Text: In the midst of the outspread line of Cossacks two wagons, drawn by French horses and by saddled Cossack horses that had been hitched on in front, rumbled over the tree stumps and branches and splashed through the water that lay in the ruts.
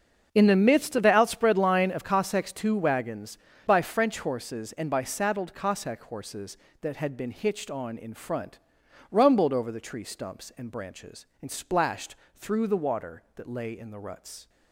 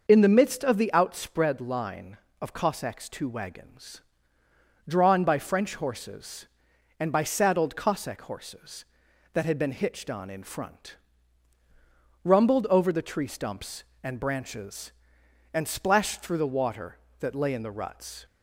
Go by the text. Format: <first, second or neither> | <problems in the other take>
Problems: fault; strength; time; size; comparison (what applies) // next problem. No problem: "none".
second | starts louder than the rest; until 1.3 s; 6.5 dB; noticeable in the second // skips "drawn"; at 3.5 s // pauses between "splashed" and "through"; slight; at 12.1 s; 0.20 s long